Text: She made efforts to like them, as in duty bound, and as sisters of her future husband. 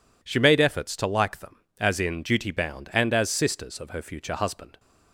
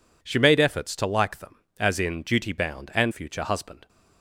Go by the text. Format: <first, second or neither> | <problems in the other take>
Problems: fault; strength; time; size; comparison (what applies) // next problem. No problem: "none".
first | skips "as sisters of her"; at 3.1 s